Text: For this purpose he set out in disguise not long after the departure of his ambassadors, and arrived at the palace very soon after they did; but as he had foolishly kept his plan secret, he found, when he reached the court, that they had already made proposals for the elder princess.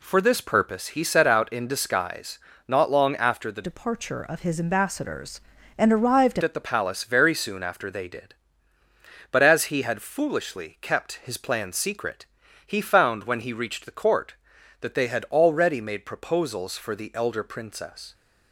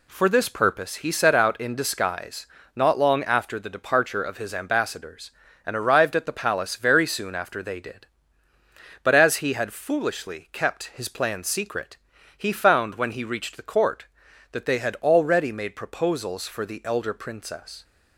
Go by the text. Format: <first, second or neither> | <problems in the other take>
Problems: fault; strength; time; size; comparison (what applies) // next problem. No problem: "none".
second | pauses between "disguise" and "not"; slight; at 2.3 s; 0.30 s long; slight in the second // changes voice from "departure" to "arrived"; from 3.6 to 6.3 s; 2.7 s long